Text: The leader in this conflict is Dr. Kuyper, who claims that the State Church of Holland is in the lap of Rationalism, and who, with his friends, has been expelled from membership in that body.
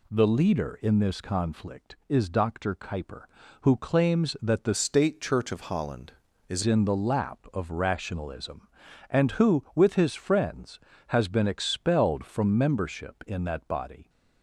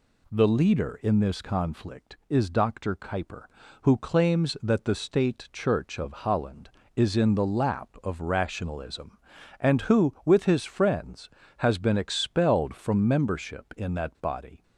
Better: second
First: changes voice from "State" to "is"; from 4.7 to 6.6 s; 1.9 s long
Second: none

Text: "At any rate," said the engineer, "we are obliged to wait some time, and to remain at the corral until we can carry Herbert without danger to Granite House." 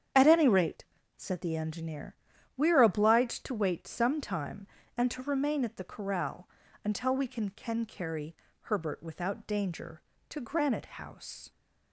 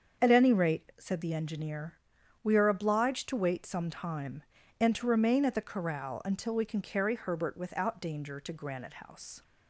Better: second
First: starts louder than the rest; strong; until 1.4 s; 8.5 dB // pauses between "corral" and "until"; slight; at 6.4 s; 0.34 s long // says "can" twice; at 7.5 s // pauses between "carry" and "Herbert"; slight; at 8.3 s; 0.26 s long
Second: starts louder than the rest; until 1.2 s; 7 dB

